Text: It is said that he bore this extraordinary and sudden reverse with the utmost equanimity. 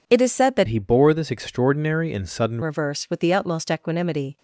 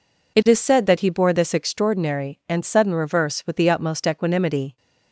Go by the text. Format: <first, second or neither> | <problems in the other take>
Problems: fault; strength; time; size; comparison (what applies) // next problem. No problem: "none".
second | changes voice from "he" to "sudden"; from 0.6 to 2.5 s; 1.9 s long